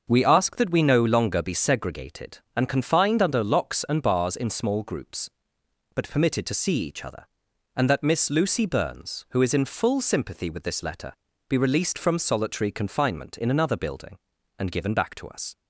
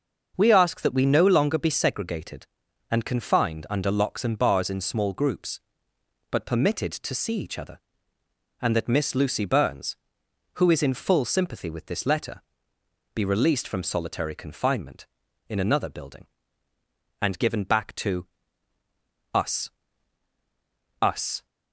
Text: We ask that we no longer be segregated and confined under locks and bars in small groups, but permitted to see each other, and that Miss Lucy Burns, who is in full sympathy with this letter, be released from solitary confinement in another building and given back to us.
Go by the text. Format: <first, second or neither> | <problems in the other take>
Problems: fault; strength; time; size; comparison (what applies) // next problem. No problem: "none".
first | starts louder than the rest; until 1.3 s; 6.5 dB; also in the first // pauses between "to" and "us"; at 18.2 s; 1.0 s long // says "us" twice; at 21.0 s